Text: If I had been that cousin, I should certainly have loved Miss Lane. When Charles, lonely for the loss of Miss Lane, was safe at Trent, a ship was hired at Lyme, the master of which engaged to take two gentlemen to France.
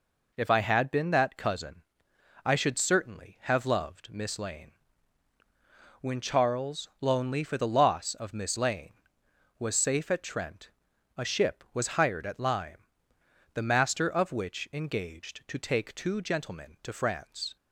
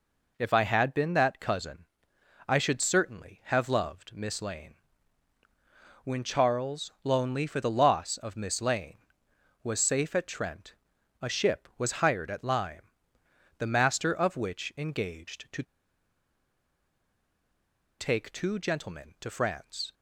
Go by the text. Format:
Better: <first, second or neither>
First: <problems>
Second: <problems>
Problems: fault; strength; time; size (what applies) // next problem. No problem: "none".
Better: first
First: none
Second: pauses between "to" and "take"; strong; at 15.6 s; 2.3 s long